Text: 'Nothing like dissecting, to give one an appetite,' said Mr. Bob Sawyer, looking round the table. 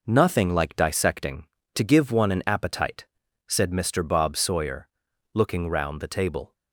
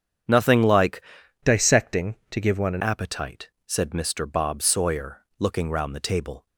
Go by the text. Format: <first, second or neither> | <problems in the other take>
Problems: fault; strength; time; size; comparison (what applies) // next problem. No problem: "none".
first | starts louder than the rest; strong; until 1.7 s; 8 dB // changes voice from "dissecting" to "an"; from 1.4 to 2.8 s; 1.4 s long